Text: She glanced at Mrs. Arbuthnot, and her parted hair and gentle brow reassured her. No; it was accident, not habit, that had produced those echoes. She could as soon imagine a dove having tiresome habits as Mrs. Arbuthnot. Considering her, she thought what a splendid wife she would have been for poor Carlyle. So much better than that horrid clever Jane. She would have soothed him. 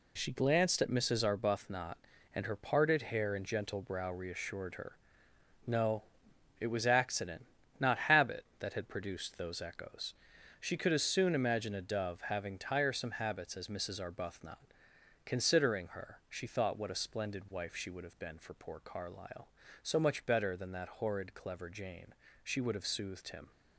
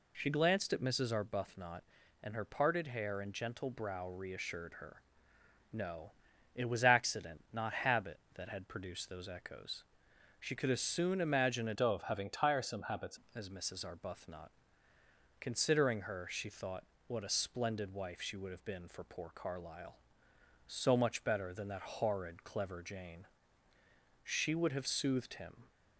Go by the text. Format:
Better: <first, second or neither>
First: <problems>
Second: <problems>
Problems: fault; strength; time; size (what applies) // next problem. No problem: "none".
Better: first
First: none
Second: changes voice from "dove" to "habits"; from 11.7 to 13.1 s; 1.4 s long // pauses between "thought" and "what"; slight; at 16.8 s; 0.24 s long